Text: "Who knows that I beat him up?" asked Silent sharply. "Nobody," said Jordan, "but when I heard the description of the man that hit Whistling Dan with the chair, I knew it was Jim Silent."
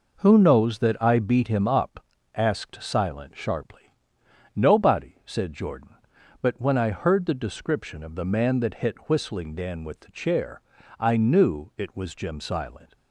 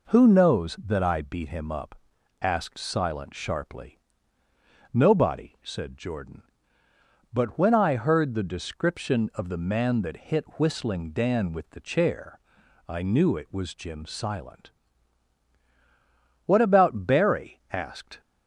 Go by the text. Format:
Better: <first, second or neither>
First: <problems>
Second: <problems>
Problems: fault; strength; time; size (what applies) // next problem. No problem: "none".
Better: first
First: none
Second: goes on to say "What about Barry asked"; strong; from 16.4 s on; 1.7 s long